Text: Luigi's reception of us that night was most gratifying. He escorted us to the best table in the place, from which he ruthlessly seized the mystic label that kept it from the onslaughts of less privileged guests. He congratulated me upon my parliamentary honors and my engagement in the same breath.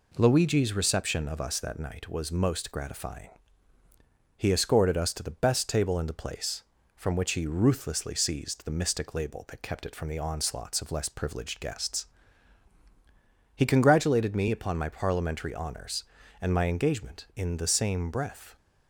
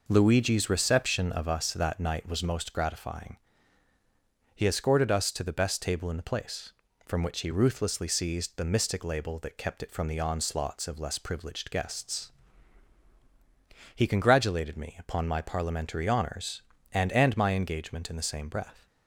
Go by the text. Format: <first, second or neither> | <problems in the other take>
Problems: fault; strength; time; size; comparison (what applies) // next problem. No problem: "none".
first | says "and" twice; at 17.1 s